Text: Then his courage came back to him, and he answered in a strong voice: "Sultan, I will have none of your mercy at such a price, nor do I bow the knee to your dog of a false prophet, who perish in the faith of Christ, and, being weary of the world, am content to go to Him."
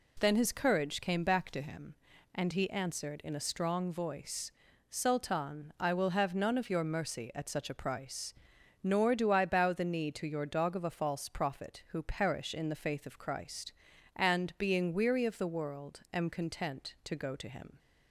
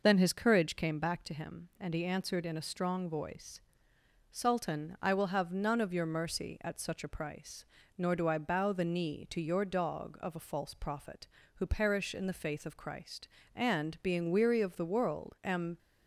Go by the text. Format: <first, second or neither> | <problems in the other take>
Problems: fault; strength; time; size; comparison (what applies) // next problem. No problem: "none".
first | stops before "content to go to Him"; at 15.7 s